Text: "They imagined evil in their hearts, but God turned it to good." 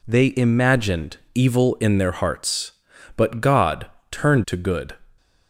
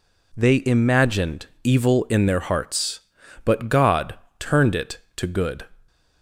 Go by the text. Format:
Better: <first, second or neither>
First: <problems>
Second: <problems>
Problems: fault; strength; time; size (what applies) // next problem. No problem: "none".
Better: second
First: pauses between "imagined" and "evil"; slight; at 1.1 s; 0.18 s long // pauses between "God" and "turned"; slight; at 3.8 s; 0.24 s long // skips "it"; at 4.4 s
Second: pauses between "imagined" and "evil"; slight; at 1.4 s; 0.18 s long // pauses between "God" and "turned"; slight; at 4.1 s; 0.24 s long